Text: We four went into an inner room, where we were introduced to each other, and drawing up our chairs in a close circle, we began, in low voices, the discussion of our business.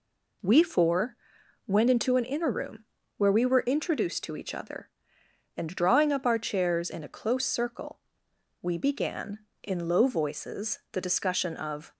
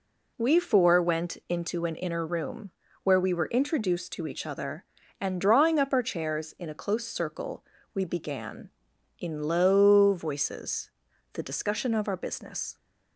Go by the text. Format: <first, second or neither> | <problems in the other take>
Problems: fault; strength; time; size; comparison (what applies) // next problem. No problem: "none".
second | pauses between "four" and "went"; noticeable; at 1.1 s; 0.50 s long // stops before "our business"; at 11.9 s